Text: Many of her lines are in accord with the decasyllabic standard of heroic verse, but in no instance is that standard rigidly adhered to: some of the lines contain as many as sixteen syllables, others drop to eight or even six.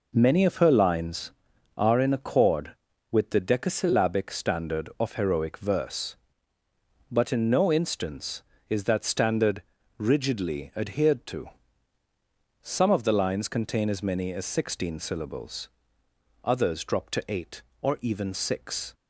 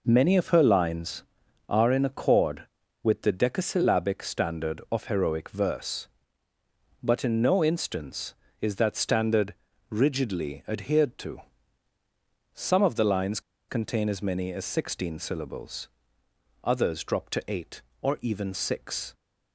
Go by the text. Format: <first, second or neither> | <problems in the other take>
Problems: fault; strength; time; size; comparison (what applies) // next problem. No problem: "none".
first | pauses between "standard" and "rigidly"; slight; at 9.5 s; 0.34 s long; slight in the first // pauses between "lines" and "contain"; slight; at 13.3 s; 0.29 s long